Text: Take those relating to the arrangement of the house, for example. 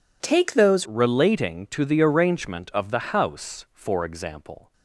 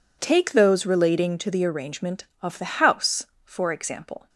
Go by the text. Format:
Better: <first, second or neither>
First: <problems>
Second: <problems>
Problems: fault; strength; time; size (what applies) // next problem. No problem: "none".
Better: second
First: changes voice at "relating"; from 0.8 s on; 3.9 s long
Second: none